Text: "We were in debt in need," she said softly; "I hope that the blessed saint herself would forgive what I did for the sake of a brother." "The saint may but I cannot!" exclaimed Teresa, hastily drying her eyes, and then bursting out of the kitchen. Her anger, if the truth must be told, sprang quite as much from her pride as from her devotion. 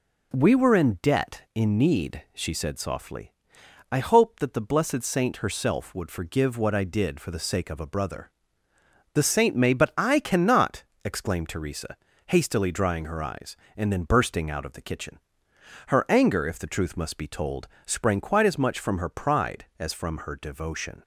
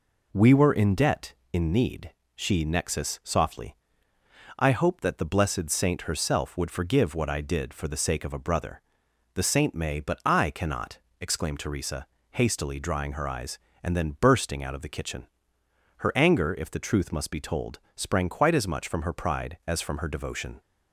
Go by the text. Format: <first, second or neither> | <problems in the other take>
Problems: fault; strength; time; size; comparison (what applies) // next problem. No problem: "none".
first | says "nexus" for "said"; at 2.6 s